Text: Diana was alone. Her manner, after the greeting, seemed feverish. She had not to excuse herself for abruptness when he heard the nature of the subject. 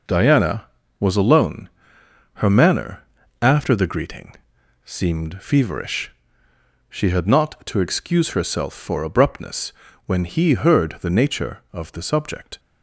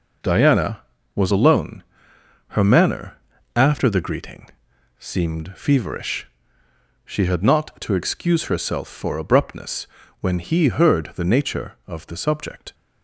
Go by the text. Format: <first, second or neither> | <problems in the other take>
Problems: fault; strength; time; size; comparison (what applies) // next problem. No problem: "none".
neither | pauses between "abruptness" and "when"; slight; the same in both